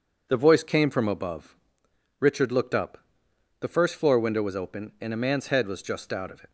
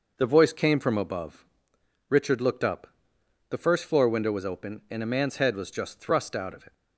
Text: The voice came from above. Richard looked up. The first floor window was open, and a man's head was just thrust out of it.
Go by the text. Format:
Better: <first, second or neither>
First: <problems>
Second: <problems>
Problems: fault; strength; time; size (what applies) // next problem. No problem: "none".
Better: second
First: skips "thrust"; at 6.1 s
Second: none